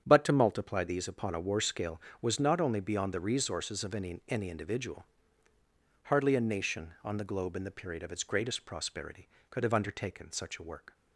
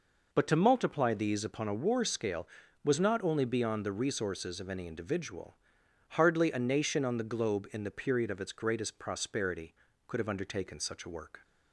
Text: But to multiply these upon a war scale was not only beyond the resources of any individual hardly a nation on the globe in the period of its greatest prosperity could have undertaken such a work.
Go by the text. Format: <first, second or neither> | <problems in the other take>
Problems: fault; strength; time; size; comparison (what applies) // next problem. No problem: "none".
second | starts louder than the rest; strong; until 1.0 s; 8.5 dB // says "any" twice; at 4.2 s // pauses between "individual" and "hardly"; at 5.0 s; 1.0 s long; noticeable in the second